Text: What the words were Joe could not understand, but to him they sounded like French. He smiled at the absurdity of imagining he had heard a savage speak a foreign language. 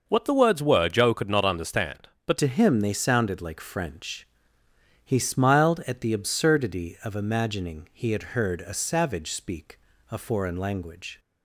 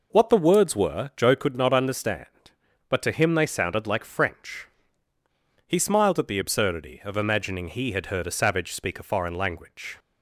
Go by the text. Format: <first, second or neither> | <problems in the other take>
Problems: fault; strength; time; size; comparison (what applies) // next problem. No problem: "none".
second | changes voice at "to"; from 2.3 s on; 8.8 s long // pauses between "speak" and "a"; slight; at 9.7 s; 0.30 s long